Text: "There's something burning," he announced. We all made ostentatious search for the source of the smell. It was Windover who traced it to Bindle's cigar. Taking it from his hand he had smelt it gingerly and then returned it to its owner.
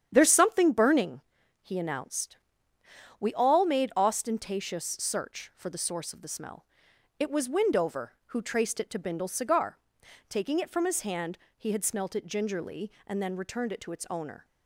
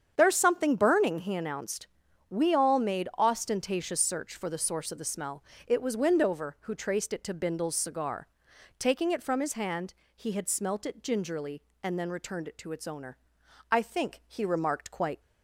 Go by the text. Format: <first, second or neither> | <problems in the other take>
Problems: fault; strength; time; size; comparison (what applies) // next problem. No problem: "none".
first | starts louder than the rest; strong; until 1.1 s; 8 dB; strong in the first // pauses between "hand" and "he"; slight; at 9.9 s; 0.22 s long; slight in the first // goes on to say "I think he remarked quite"; from 13.6 s on; 1.5 s long